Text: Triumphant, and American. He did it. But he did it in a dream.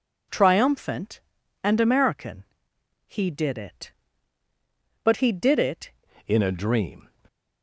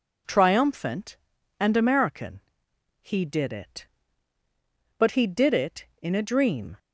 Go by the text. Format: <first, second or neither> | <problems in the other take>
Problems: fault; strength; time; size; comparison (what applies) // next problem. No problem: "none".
second | changes voice at "in"; from 6.2 s on; 0.8 s long